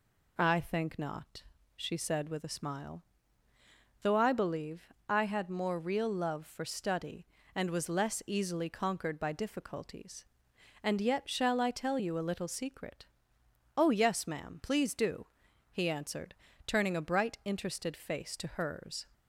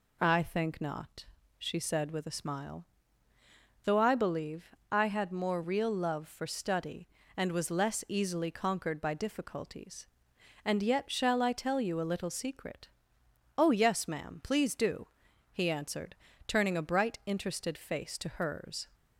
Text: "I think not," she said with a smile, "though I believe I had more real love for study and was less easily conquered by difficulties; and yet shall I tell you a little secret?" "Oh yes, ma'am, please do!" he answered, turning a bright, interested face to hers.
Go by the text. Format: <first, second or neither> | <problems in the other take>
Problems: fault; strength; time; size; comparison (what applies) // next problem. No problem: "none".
neither | pauses between "believe" and "I"; slight; the same in both